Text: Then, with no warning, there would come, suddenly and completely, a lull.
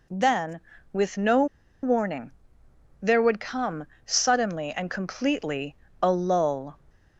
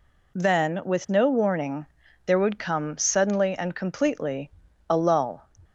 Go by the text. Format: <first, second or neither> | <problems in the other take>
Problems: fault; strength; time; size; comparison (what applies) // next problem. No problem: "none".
second | pauses between "no" and "warning"; at 1.4 s; 0.37 s long